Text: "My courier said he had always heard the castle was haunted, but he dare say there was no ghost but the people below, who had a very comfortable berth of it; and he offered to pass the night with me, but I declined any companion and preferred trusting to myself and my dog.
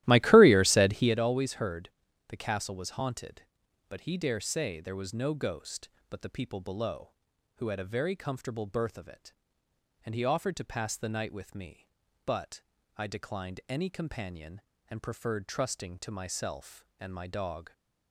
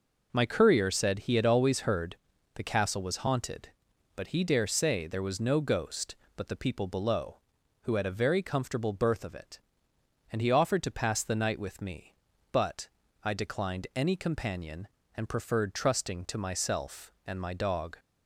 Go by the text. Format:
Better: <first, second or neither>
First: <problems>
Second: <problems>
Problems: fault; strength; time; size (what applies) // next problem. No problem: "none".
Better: second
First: starts louder than the rest; strong; until 1.2 s; 15.5 dB // pauses between "heard" and "the"; at 1.8 s; 0.40 s long // pauses between "but" and "I"; slight; at 12.6 s; 0.34 s long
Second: pauses between "heard" and "the"; at 2.1 s; 0.40 s long // pauses between "but" and "I"; slight; at 12.8 s; 0.34 s long